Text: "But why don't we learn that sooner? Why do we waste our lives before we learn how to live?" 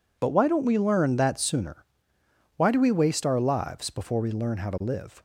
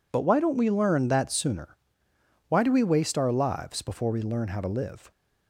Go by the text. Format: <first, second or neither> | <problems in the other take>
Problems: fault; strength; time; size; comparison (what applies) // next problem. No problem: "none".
neither | none